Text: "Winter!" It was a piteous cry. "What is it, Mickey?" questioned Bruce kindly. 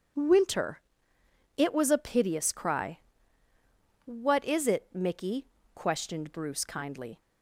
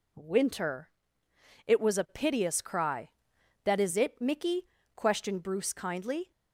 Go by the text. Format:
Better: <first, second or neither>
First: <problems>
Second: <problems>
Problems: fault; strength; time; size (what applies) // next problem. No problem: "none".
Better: first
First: none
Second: says "That" for "What"; at 3.6 s